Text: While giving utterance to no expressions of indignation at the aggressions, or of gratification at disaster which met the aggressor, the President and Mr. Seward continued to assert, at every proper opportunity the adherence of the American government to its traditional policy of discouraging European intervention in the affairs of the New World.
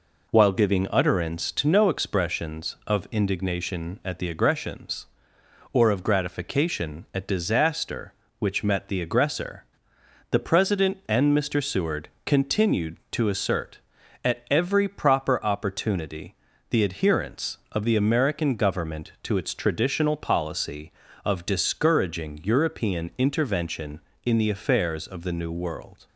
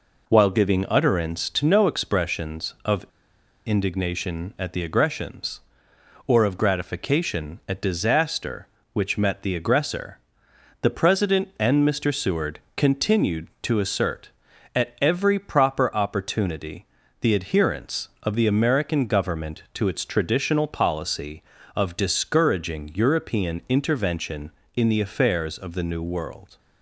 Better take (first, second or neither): first